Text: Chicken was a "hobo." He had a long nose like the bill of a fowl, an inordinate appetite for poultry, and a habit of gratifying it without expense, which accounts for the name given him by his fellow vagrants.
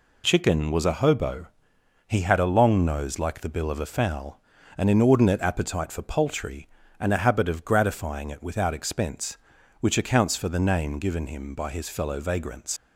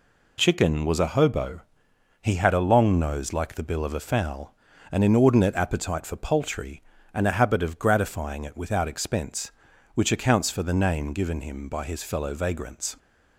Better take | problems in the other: second | leaves "vagrants" unfinished; at 12.7 s; 75 ms

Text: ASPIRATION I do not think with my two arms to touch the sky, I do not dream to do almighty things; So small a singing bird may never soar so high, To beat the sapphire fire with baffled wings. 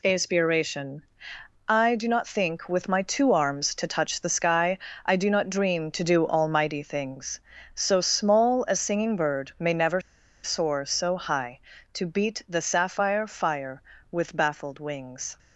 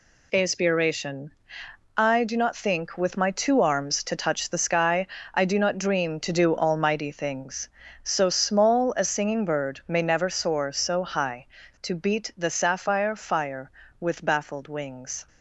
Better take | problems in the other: second | pauses between "ASPIRATION" and "I"; noticeable; at 1.0 s; 0.64 s long; noticeable in the second // pauses between "never" and "soar"; at 10.0 s; 0.43 s long

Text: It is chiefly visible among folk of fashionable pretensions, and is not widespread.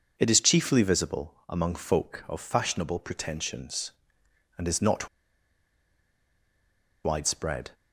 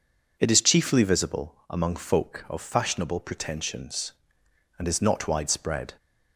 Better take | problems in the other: second | pauses between "not" and "widespread"; strong; at 5.0 s; 1.9 s long

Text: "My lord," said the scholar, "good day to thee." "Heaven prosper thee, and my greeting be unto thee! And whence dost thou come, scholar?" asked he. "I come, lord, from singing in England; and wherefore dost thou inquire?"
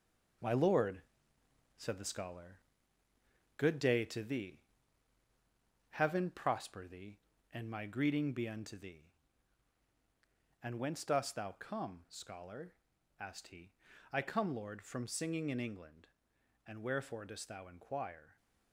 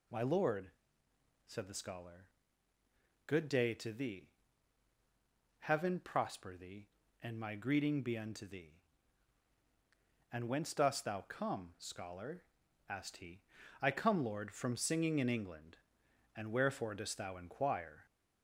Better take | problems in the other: second | gets quieter; noticeable; throughout; 6 dB

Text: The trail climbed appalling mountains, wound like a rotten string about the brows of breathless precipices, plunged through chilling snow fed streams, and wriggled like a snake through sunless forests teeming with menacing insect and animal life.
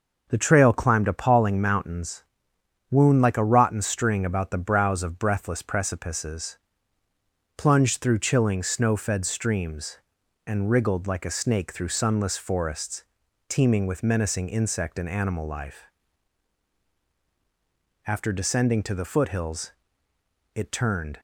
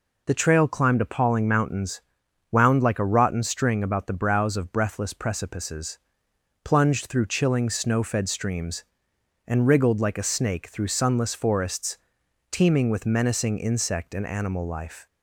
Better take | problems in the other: second | starts louder than the rest; until 1.3 s; 6 dB // pauses between "forests" and "teeming"; at 13.0 s; 0.44 s long; noticeable in the second // goes on to say "After descending to the foothills it turned"; strong; from 18.0 s on; 3.1 s long

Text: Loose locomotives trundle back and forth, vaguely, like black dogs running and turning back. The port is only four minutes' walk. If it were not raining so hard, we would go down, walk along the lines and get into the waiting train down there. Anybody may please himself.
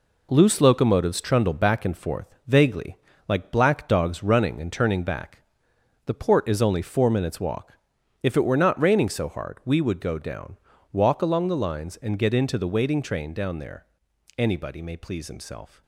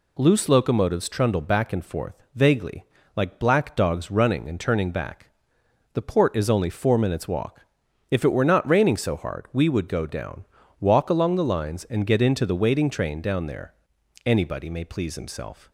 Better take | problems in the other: second | gets quieter; strong; throughout; 7.5 dB

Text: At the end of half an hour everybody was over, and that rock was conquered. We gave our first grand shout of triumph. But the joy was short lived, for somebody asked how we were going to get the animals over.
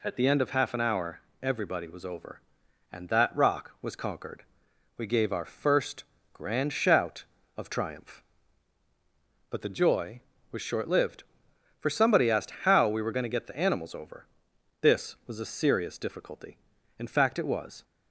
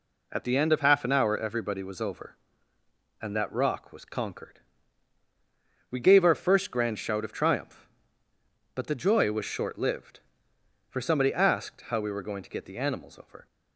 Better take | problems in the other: second | pauses between "hour" and "everybody"; slight; at 1.1 s; 0.24 s long // pauses between "first" and "grand"; slight; at 6.0 s; 0.28 s long // goes on to say "This was a serious difficulty in fact it was"; strong; from 14.8 s on; 3.0 s long

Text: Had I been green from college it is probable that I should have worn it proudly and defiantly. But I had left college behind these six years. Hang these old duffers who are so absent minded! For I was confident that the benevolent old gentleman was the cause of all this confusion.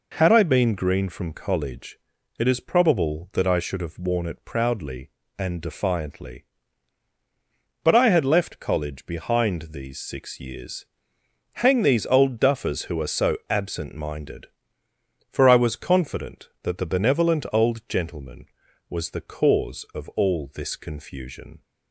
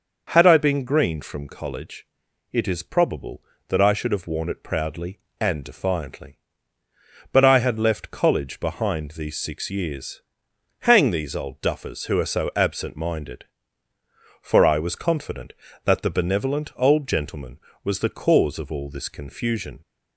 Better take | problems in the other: neither | pauses between "college" and "it"; the same in both

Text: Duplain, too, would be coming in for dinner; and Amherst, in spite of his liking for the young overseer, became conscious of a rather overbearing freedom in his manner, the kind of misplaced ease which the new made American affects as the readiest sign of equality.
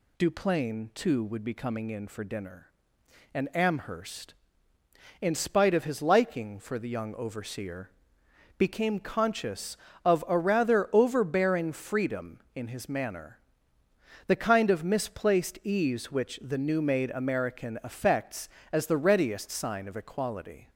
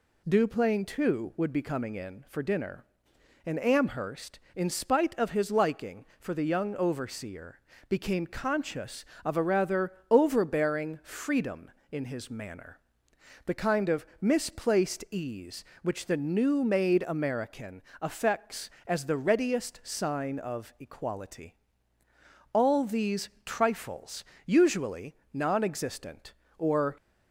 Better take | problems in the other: first | pauses between "rather" and "overbearing"; slight; at 9.9 s; 0.18 s long // pauses between "American" and "affects"; slight; at 17.8 s; 0.18 s long // goes on to say "All these trifles usually non existent or"; strong; from 22.5 s on; 4.4 s long

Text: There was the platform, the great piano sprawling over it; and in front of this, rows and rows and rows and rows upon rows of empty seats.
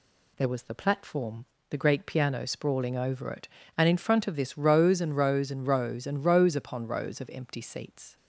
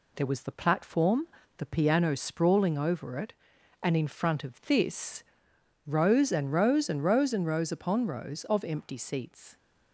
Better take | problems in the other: first | skips "great"; at 1.6 s

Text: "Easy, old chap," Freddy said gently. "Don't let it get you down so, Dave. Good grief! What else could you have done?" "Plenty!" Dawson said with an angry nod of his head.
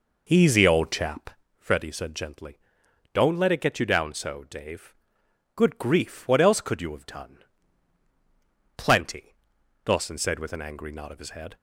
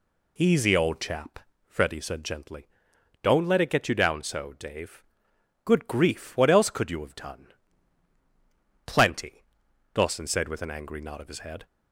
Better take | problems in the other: second | starts louder than the rest; noticeable; until 1.5 s; 5 dB

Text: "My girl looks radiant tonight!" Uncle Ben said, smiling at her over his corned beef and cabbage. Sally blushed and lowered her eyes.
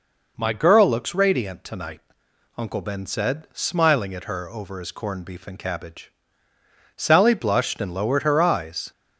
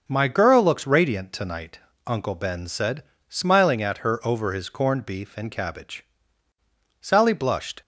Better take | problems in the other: first | starts louder than the rest; until 1.0 s; 6 dB // stops before "and lowered her eyes"; at 7.8 s

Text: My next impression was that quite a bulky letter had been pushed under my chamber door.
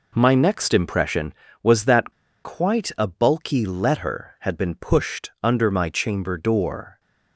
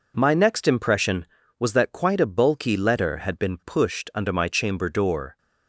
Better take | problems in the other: second | pauses between "that" and "quite"; slight; at 2.1 s; 0.31 s long

